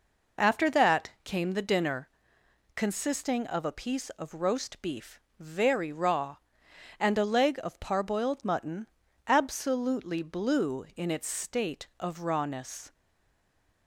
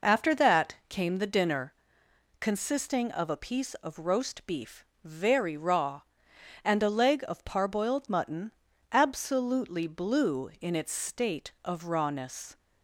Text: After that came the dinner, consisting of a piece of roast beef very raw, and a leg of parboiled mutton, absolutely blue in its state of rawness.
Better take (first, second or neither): second